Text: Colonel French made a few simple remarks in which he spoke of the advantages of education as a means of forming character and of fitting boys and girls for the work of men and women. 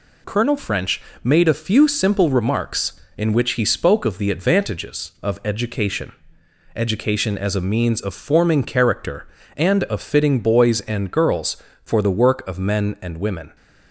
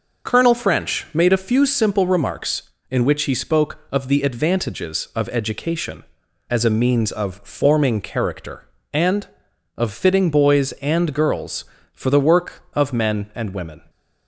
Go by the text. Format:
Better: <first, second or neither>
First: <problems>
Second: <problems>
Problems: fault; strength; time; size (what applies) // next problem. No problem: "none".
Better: second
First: pauses between "French" and "made"; slight; at 1.0 s; 0.22 s long // says "education" twice; at 6.7 s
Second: none